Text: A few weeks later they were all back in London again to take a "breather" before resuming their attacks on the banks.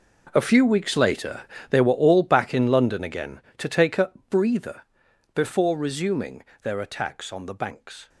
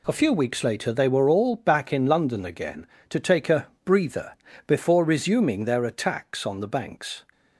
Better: second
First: gets quieter; strong; throughout; 16.5 dB // pauses between "later" and "they"; slight; at 1.4 s; 0.28 s long // pauses between "a" and "breather"; slight; at 4.0 s; 0.18 s long // pauses between "breather" and "before"; noticeable; at 4.8 s; 0.52 s long // pauses between "resuming" and "their"; slight; at 6.4 s; 0.20 s long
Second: pauses between "a" and "breather"; slight; at 3.6 s; 0.18 s long // pauses between "breather" and "before"; slight; at 4.3 s; 0.34 s long

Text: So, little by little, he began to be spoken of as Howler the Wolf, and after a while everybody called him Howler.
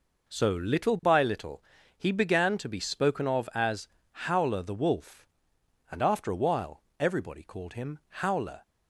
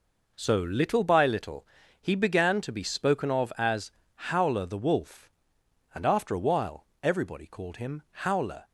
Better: neither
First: pauses between "as" and "Howler"; slight; at 3.8 s; 0.24 s long // pauses between "while" and "everybody"; slight; at 6.8 s; 0.18 s long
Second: pauses between "as" and "Howler"; slight; at 3.9 s; 0.24 s long // pauses between "while" and "everybody"; slight; at 6.8 s; 0.18 s long

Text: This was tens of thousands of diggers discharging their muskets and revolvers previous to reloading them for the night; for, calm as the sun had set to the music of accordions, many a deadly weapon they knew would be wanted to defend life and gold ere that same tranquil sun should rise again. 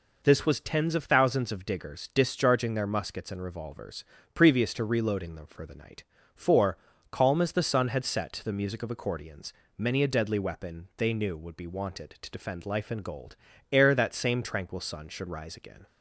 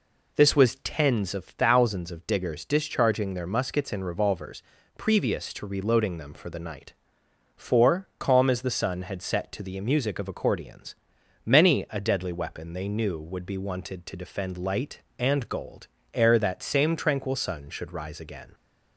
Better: first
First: pauses between "revolvers" and "previous"; slight; at 4.0 s; 0.30 s long // pauses between "gold" and "ere"; slight; at 13.3 s; 0.36 s long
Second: pauses between "revolvers" and "previous"; slight; at 4.6 s; 0.34 s long // says "light" for "life"; at 14.5 s // pauses between "gold" and "ere"; slight; at 15.8 s; 0.28 s long

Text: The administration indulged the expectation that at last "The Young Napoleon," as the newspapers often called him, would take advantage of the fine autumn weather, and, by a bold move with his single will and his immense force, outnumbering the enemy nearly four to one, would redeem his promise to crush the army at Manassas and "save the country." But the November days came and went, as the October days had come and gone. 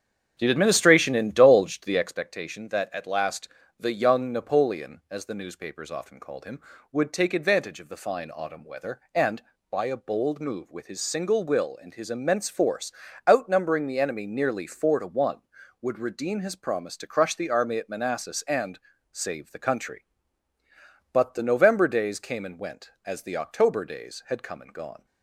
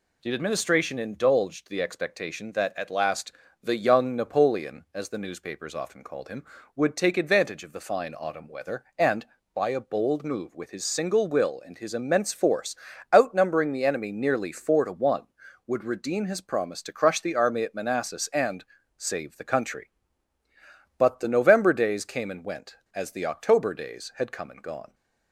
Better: second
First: starts louder than the rest; strong; until 2.2 s; 8 dB // pauses between "last" and "The"; slight; at 3.4 s; 0.32 s long // pauses between "and" and "save"; slight; at 18.7 s; 0.36 s long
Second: pauses between "last" and "The"; slight; at 3.3 s; 0.32 s long // pauses between "and" and "save"; slight; at 18.6 s; 0.36 s long

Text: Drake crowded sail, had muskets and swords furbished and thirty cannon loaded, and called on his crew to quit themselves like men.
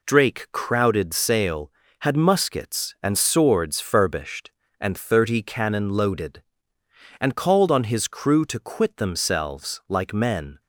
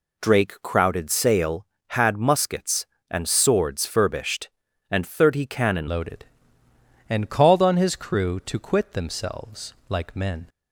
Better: first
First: none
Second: changes voice at "loaded"; from 5.8 s on; 4.6 s long // pauses between "themselves" and "like"; slight; at 9.7 s; 0.16 s long

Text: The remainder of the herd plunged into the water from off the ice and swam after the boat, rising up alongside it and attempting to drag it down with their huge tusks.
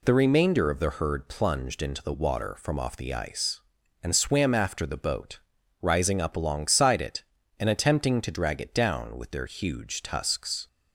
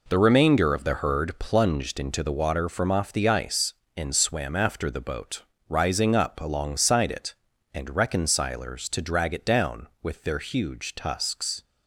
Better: first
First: none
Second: says "reconcilers" for "attempting"; at 7.9 s

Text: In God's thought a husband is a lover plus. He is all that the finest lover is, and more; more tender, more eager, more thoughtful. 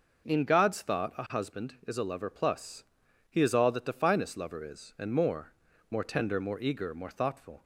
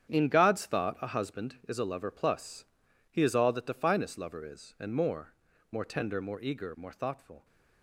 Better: first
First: none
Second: gets quieter; strong; throughout; 12 dB

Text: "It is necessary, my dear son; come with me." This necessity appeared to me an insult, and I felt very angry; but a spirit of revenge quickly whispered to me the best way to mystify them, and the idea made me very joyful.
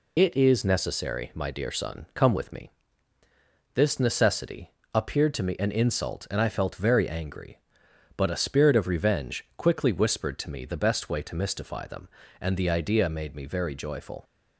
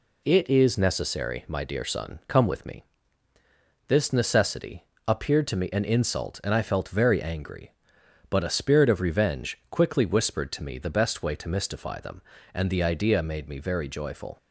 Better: second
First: loses the start of "It"; at 0.1 s; 55 ms // pauses between "necessity" and "appeared"; slight; at 4.7 s; 0.22 s long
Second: pauses between "necessity" and "appeared"; slight; at 4.8 s; 0.22 s long

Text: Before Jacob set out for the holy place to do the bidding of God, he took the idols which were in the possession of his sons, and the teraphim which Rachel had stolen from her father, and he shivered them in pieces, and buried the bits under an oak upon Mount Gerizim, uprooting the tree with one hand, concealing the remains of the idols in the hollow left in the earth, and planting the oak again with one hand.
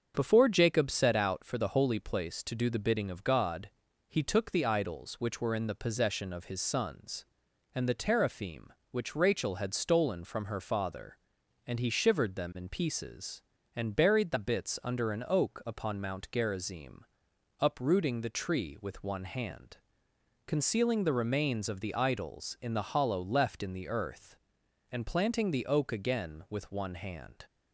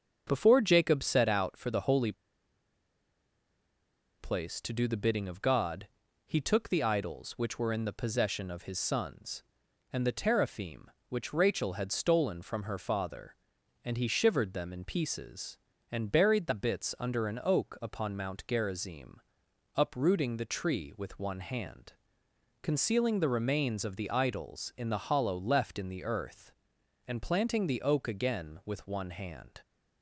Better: first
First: starts louder than the rest; until 1.1 s; 7 dB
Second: starts louder than the rest; until 1.2 s; 6.5 dB // pauses between "holy" and "place"; strong; at 2.1 s; 2.0 s long

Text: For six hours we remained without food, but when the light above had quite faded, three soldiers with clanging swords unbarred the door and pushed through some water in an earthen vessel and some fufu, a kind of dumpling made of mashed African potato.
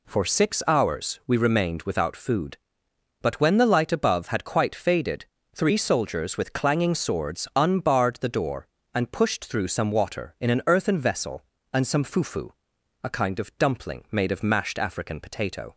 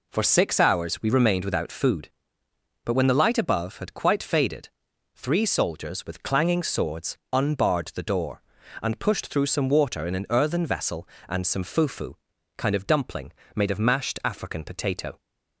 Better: first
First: none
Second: skips "a"; at 12.3 s // pauses between "dumpling" and "made"; slight; at 13.3 s; 0.22 s long

